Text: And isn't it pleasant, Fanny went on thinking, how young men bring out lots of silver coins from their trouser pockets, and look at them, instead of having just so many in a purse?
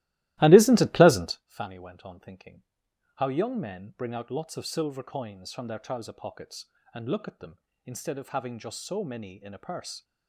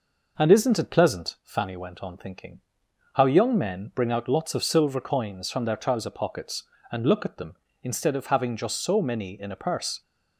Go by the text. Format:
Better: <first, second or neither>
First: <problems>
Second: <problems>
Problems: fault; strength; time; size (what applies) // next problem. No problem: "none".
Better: second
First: starts louder than the rest; strong; until 1.4 s; 16.5 dB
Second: none